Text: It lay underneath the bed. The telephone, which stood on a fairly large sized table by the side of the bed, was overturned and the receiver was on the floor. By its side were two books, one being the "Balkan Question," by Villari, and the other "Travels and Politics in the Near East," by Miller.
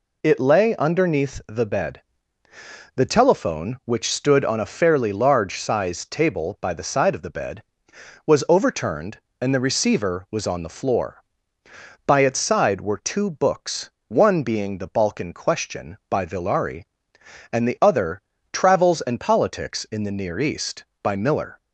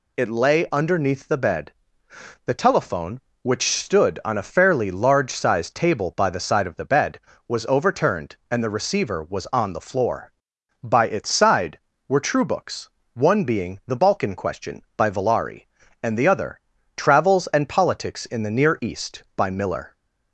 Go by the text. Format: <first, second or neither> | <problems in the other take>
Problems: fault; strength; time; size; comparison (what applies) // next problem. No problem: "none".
first | says "true" for "two"; at 12.1 s // pauses between "other" and "Travels"; at 16.5 s; 0.38 s long; slight in the first